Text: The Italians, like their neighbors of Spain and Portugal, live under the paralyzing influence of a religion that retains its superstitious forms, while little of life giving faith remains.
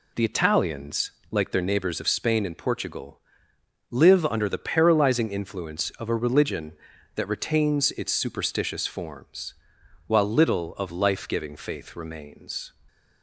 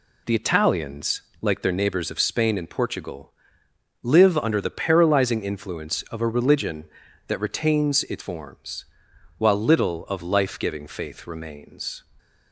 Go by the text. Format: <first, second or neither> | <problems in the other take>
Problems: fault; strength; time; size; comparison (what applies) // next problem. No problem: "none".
first | skips "superstitious"; at 8.2 s